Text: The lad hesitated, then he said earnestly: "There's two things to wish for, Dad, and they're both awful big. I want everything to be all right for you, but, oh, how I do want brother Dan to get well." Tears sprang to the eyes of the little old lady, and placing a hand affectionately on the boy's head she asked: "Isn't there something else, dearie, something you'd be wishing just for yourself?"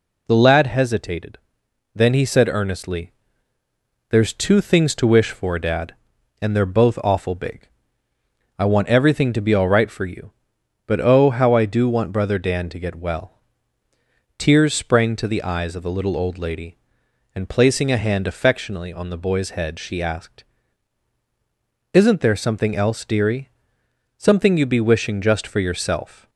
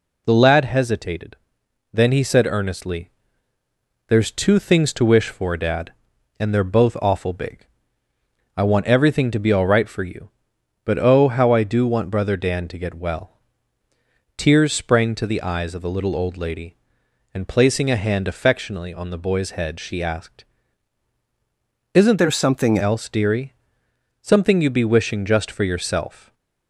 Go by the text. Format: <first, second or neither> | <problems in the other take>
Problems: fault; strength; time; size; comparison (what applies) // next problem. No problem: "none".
first | changes voice from "there" to "something"; from 22.1 to 22.7 s; 0.6 s long // stays silent after the last word; slight; from 26.1 s on; 0.5 s long